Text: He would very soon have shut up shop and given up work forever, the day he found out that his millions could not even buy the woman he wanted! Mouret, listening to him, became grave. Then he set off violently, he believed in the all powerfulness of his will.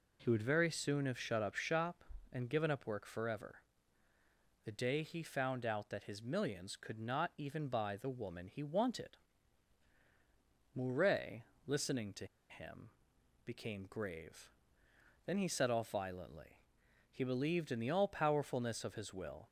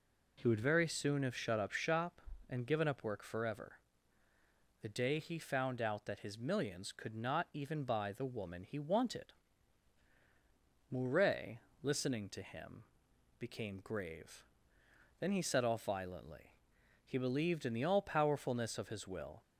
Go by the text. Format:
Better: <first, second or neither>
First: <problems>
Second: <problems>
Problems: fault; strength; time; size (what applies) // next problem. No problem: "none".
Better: second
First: pauses between "to" and "him"; slight; at 12.2 s; 0.22 s long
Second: none